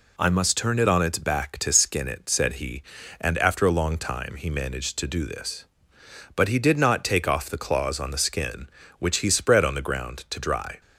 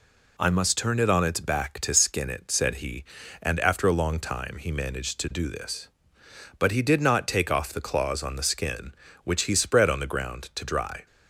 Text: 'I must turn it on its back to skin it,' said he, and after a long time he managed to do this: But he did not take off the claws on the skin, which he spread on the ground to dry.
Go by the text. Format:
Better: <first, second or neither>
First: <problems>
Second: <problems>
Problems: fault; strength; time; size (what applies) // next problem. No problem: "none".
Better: neither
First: none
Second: none